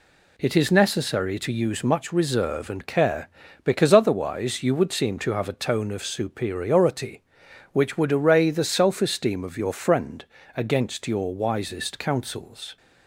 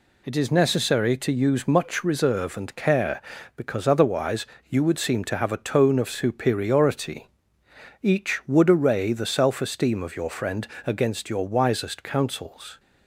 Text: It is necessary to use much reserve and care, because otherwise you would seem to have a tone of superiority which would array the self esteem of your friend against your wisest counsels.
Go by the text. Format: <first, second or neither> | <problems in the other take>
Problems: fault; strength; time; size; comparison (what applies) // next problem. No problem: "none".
first | pauses between "otherwise" and "you"; slight; at 4.4 s; 0.22 s long // says "each" for "which"; at 8.0 s // pauses between "friend" and "against"; slight; at 10.6 s; 0.18 s long; slight in the first